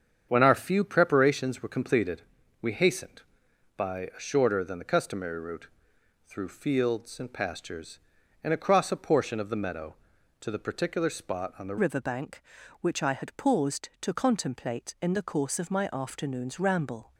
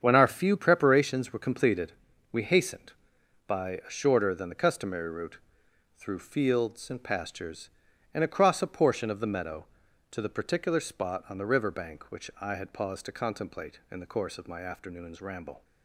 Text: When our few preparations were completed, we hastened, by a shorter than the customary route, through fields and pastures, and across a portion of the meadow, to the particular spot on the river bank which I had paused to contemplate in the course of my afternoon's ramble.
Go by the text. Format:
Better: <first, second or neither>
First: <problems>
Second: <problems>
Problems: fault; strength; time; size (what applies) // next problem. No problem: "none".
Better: second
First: starts louder than the rest; strong; until 1.3 s; 7.5 dB // changes voice at "river"; from 11.7 s on; 5.4 s long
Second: starts louder than the rest; strong; until 1.0 s; 7.5 dB